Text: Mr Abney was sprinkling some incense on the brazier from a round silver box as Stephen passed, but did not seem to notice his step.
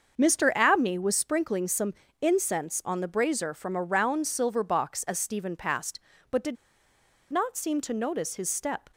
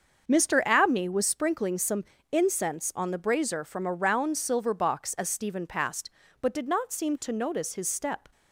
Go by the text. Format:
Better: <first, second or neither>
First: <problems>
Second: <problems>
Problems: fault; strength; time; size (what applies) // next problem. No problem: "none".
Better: second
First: starts louder than the rest; until 1.1 s; 6.5 dB // pauses between "some" and "incense"; slight; at 1.9 s; 0.28 s long // pauses between "did" and "not"; noticeable; at 6.5 s; 0.76 s long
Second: starts louder than the rest; until 1.3 s; 6.5 dB // pauses between "some" and "incense"; slight; at 2.0 s; 0.28 s long